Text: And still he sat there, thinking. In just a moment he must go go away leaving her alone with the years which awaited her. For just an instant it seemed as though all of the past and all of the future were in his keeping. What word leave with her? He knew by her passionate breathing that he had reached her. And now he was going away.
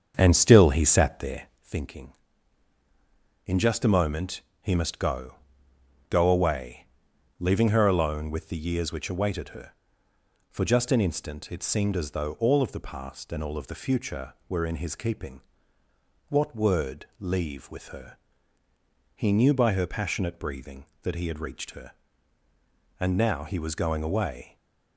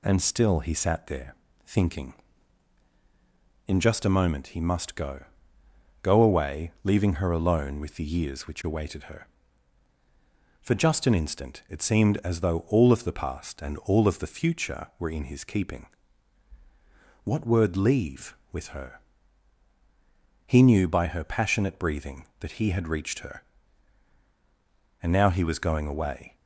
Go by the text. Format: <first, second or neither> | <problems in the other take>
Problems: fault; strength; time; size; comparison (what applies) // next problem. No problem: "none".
second | starts louder than the rest; strong; until 1.7 s; 7 dB // pauses between "moment" and "he"; slight; at 4.4 s; 0.20 s long // pauses between "go" and "go"; noticeable; at 5.3 s; 0.74 s long; noticeable in the second // pauses between "away" and "leaving"; noticeable; at 6.8 s; 0.50 s long // stays silent after the last word; slight; from 24.4 s on; 0.5 s long